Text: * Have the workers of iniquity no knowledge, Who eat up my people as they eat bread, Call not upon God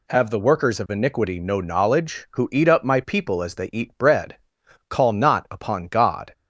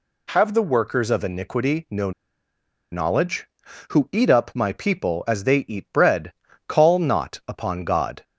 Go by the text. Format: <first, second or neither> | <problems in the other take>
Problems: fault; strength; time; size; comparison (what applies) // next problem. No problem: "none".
first | pauses between "no" and "knowledge"; noticeable; at 2.1 s; 0.81 s long